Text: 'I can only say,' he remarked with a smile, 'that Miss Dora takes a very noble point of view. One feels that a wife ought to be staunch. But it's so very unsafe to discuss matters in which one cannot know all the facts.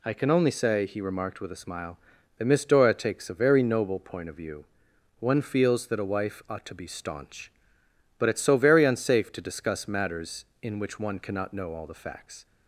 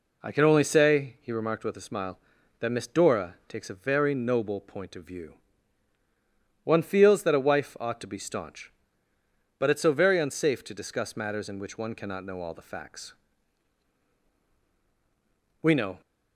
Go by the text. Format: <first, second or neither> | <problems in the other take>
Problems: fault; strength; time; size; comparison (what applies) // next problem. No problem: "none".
first | goes on to say "We know"; slight; from 15.6 s on; 0.38 s long